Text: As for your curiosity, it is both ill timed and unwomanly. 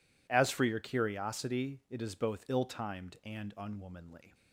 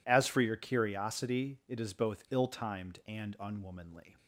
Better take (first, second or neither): neither